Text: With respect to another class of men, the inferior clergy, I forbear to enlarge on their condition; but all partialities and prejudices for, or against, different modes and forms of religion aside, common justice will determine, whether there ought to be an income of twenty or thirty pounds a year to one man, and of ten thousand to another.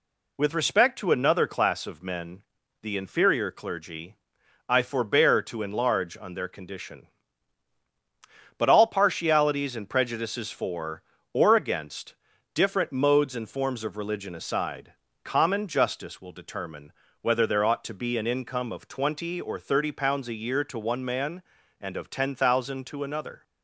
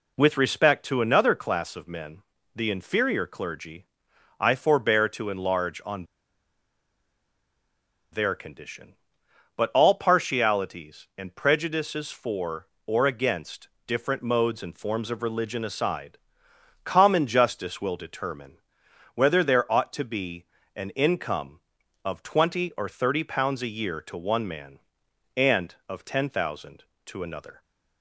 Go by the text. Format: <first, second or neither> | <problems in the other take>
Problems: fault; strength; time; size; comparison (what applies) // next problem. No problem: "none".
first | pauses between "on" and "their"; strong; at 6.0 s; 2.0 s long // pauses between "be" and "an"; slight; at 20.4 s; 0.32 s long